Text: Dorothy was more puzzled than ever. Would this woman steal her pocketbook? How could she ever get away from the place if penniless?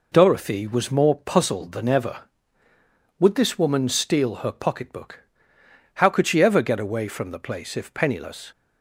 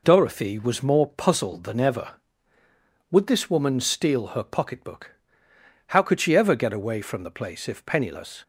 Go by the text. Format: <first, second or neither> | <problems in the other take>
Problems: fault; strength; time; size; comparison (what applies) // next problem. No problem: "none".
neither | none